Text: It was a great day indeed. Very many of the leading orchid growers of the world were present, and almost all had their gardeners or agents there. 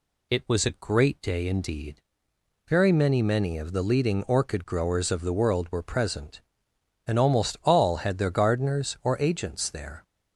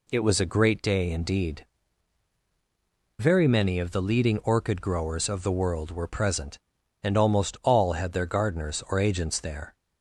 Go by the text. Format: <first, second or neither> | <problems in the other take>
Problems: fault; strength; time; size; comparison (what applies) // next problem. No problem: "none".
second | says "many" twice; at 3.2 s